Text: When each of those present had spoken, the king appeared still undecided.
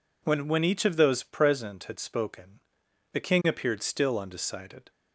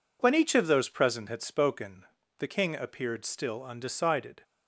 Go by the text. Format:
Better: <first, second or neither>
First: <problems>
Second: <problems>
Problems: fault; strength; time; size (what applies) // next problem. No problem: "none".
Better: second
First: says "When" twice; at 0.4 s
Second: none